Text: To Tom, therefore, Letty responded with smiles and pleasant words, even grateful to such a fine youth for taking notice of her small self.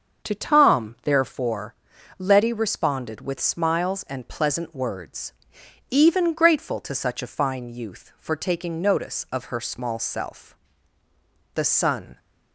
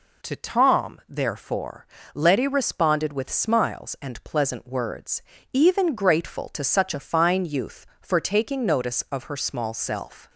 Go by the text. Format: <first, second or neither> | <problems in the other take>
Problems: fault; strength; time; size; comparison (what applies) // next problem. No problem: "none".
second | starts louder than the rest; until 1.3 s; 6.5 dB // goes on to say "The sun"; noticeable; from 11.5 s on; 0.64 s long